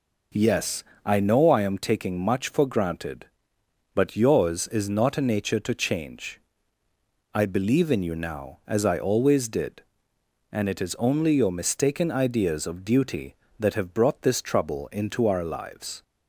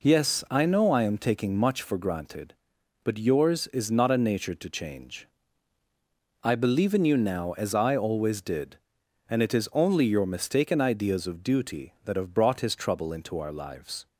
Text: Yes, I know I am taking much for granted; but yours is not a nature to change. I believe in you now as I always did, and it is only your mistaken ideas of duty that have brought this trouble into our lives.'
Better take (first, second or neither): first